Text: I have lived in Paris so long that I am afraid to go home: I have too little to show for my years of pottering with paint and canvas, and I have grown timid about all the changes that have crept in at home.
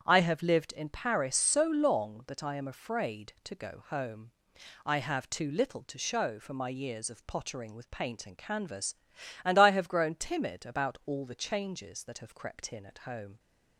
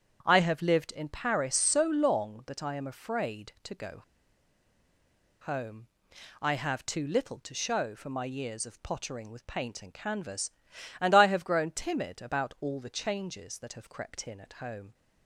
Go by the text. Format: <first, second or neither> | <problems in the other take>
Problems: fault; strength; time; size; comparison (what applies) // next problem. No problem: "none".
first | starts louder than the rest; strong; until 1.2 s; 8.5 dB; strong in the first // pauses between "go" and "home"; strong; at 4.0 s; 1.4 s long